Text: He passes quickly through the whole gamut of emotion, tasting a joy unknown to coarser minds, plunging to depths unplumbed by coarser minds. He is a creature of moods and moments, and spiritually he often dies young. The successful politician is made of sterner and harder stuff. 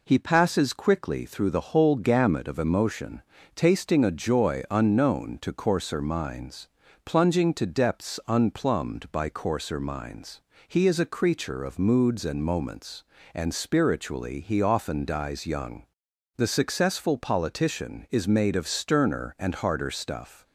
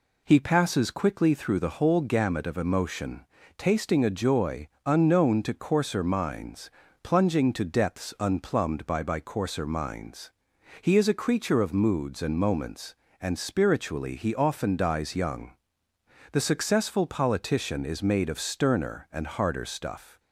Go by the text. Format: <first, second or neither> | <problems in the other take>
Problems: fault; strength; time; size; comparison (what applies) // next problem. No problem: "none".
first | pauses between "joy" and "unknown"; slight; at 4.6 s; 0.18 s long // says "by" twice; at 9.0 s